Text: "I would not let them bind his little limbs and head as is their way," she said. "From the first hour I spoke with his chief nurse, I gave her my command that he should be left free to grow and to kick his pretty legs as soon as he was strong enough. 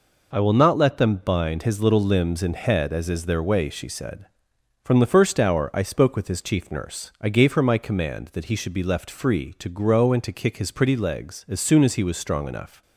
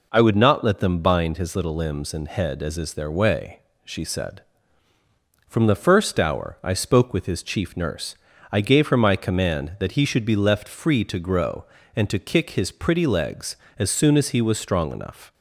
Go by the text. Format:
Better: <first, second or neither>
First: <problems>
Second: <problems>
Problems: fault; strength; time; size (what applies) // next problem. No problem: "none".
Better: second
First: says "will" for "would"; at 0.3 s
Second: none